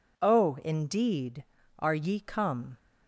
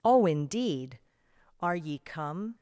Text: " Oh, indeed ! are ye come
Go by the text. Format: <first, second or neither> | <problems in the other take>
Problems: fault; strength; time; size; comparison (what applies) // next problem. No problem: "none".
neither | none